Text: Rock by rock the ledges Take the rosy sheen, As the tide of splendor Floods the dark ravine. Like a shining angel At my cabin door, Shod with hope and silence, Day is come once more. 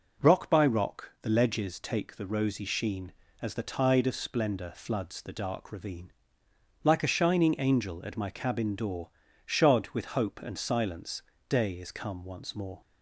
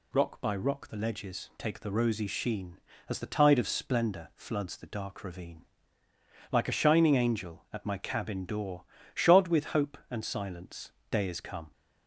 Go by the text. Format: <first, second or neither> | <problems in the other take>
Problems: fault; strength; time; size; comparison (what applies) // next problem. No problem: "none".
first | stops before "once more"; at 11.7 s